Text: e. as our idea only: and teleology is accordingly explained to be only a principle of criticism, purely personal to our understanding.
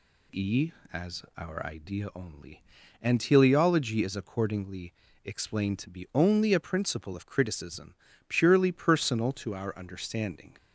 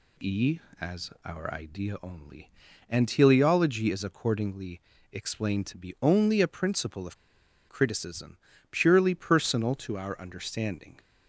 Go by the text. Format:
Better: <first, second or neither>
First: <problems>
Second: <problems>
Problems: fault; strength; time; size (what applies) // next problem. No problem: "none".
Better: first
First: pauses between "accordingly" and "explained"; slight; at 4.9 s; 0.32 s long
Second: pauses between "accordingly" and "explained"; slight; at 4.8 s; 0.32 s long // pauses between "of" and "criticism"; noticeable; at 7.1 s; 0.53 s long